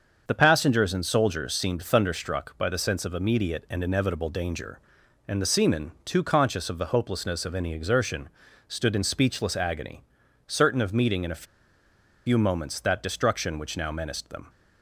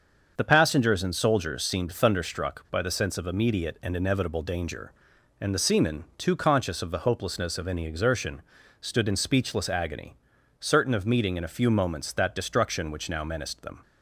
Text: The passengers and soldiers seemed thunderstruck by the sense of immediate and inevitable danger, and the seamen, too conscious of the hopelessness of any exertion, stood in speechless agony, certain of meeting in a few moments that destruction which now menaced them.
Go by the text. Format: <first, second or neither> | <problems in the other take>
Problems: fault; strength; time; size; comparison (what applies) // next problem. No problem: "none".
second | starts louder than the rest; until 1.2 s; 6.5 dB; also in the second // pauses between "a" and "few"; noticeable; at 11.4 s; 0.82 s long